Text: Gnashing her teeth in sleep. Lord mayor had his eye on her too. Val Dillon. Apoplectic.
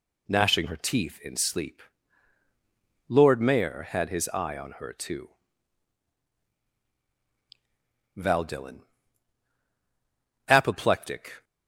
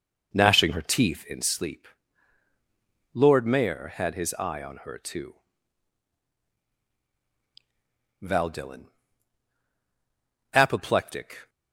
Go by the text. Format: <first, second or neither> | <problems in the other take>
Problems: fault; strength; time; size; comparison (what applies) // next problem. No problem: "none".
first | starts louder than the rest; noticeable; until 1.6 s; 4.5 dB